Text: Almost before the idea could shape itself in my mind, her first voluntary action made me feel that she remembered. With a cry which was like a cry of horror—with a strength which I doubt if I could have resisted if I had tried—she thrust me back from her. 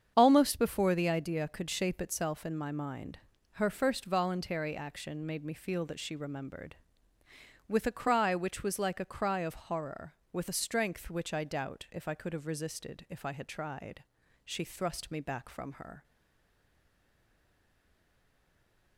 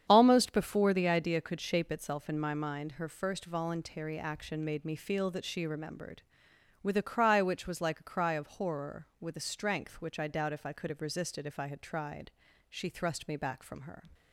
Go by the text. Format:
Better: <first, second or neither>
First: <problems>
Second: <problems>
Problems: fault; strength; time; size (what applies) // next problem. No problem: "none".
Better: second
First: starts louder than the rest; strong; until 1.1 s; 7.5 dB // stays silent after the last word; strong; from 16.0 s on; 2.9 s long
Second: starts louder than the rest; strong; until 1.1 s; 8.5 dB